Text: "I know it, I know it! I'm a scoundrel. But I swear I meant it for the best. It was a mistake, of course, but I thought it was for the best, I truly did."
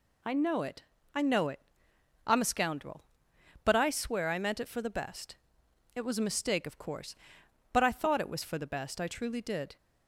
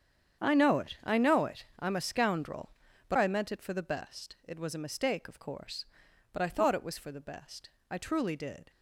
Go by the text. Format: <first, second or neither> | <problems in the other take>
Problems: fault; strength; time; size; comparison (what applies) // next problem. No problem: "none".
first | starts louder than the rest; strong; until 1.4 s; 8 dB // skips "I swear"; at 3.1 s